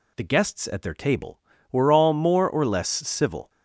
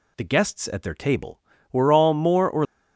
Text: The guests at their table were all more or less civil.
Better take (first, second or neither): first